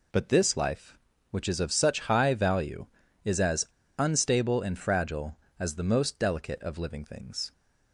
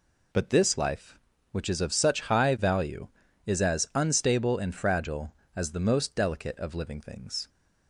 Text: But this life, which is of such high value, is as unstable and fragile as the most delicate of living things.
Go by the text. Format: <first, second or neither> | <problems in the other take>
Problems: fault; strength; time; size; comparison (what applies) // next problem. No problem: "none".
second | pauses between "as" and "unstable"; slight; at 3.6 s; 0.31 s long